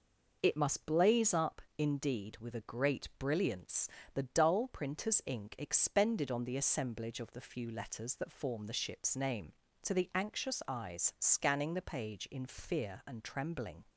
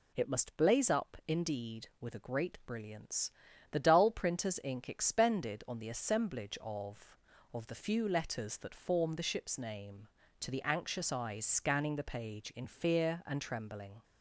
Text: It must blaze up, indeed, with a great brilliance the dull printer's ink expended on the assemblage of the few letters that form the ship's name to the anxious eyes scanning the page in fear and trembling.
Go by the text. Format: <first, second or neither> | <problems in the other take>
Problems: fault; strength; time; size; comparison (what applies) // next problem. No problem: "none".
first | pauses between "brilliance" and "the"; at 3.3 s; 0.40 s long; slight in the first // says "of" twice; at 7.5 s